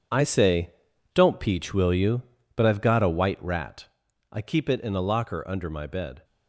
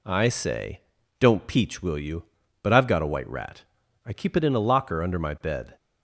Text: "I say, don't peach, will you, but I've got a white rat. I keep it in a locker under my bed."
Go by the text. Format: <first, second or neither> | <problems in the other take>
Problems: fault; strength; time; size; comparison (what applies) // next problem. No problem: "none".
second | gets quieter; strong; throughout; 12.5 dB